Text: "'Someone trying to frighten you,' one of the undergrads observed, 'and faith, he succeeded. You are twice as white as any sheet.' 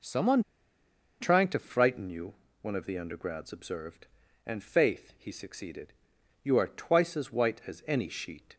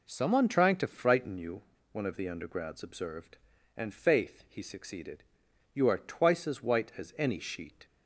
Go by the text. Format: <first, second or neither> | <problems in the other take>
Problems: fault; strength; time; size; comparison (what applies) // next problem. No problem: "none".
second | pauses between "Someone" and "trying"; noticeable; at 0.4 s; 0.79 s long